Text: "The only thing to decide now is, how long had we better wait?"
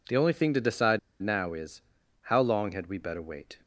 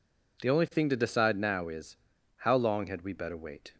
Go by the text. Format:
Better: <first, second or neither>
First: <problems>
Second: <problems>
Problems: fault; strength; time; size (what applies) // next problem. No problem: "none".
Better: second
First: pauses between "decide" and "now"; slight; at 0.9 s; 0.23 s long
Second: none